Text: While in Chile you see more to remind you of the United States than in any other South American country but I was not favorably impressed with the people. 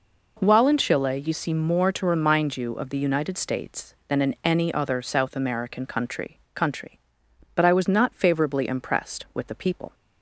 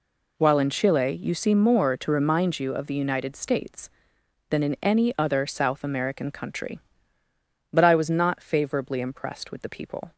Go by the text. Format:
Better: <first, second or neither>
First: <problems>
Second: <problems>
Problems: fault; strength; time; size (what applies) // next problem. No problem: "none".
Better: second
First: says "country" twice; at 6.5 s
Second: none